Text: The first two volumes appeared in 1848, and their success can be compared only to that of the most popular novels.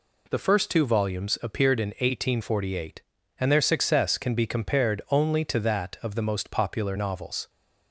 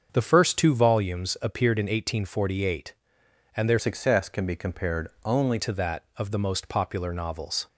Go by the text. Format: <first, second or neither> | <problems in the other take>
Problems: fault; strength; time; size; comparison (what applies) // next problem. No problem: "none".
first | starts louder than the rest; until 1.1 s; 7 dB // changes voice from "success" to "only"; from 3.7 to 5.5 s; 1.8 s long // pauses between "compared" and "only"; slight; at 5.0 s; 0.18 s long